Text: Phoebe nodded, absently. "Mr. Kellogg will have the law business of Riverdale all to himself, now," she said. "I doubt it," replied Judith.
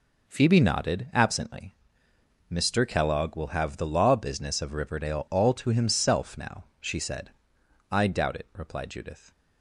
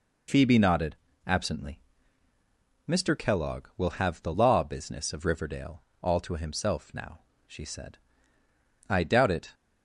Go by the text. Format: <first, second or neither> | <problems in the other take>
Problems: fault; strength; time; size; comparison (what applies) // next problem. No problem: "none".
first | pauses between "Riverdale" and "all"; slight; at 5.8 s; 0.18 s long // stops before "replied Judith"; at 9.5 s